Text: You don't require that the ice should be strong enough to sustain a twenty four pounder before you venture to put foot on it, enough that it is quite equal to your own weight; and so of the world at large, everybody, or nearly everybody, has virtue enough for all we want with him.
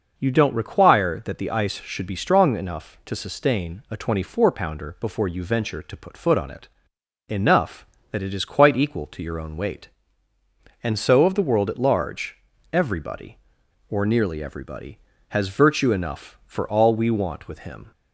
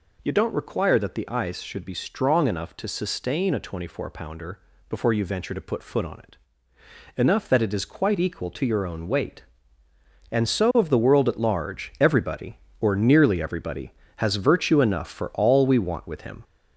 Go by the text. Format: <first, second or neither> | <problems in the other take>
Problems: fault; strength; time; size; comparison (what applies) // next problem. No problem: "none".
first | gets louder; throughout; 3.5 dB // pauses between "pounder" and "before"; slight; at 4.5 s; 0.32 s long